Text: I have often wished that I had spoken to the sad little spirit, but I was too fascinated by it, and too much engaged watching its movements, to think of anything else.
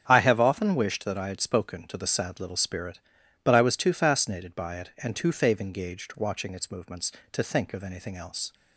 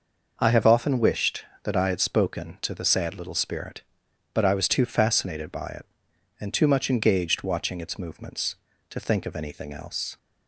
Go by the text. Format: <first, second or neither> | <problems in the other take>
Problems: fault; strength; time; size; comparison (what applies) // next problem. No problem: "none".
second | starts louder than the rest; strong; until 1.0 s; 7.5 dB // says "fave" for "much"; at 5.3 s